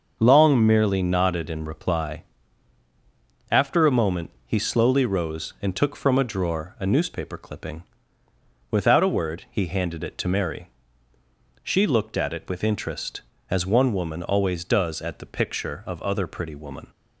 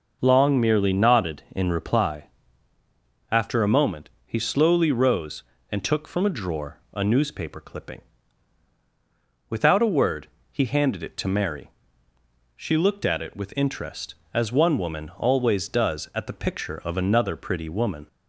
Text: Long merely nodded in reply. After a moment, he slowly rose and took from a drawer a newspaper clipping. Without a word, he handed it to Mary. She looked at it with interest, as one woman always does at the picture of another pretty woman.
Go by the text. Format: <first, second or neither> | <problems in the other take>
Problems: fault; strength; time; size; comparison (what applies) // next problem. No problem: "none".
second | starts louder than the rest; until 1.2 s; 6.5 dB // says "other" for "another"; at 16.0 s